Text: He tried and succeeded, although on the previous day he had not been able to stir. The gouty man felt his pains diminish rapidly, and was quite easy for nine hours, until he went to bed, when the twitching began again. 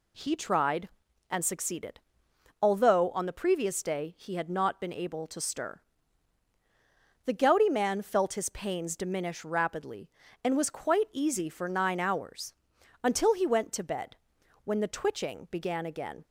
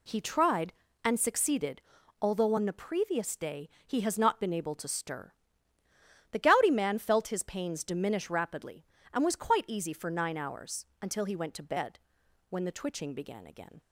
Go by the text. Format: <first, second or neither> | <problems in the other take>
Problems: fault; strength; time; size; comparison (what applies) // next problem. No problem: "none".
first | pauses between "day" and "he"; slight; at 3.6 s; 0.16 s long // says "has" for "had"; at 4.0 s